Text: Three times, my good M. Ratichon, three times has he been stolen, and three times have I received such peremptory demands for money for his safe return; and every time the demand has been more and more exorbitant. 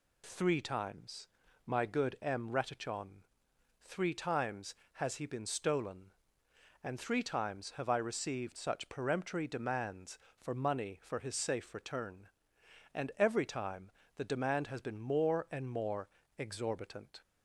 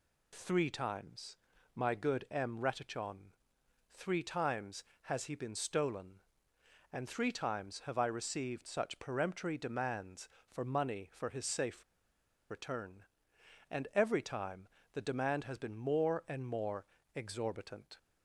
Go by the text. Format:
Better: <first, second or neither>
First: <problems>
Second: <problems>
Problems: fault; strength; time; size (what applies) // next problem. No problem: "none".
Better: first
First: pauses between "time" and "the"; slight; at 13.9 s; 0.24 s long // pauses between "more" and "exorbitant"; slight; at 16.0 s; 0.30 s long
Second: pauses between "safe" and "return"; noticeable; at 11.8 s; 0.68 s long // pauses between "time" and "the"; slight; at 14.6 s; 0.24 s long // pauses between "more" and "exorbitant"; slight; at 16.8 s; 0.30 s long